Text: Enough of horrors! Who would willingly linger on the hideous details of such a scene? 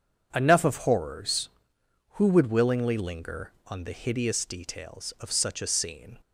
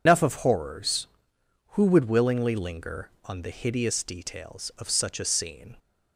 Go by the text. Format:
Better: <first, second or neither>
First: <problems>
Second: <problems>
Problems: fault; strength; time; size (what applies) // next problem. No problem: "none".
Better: first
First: none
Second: loses the start of "Enough"; at 0.0 s; 150 ms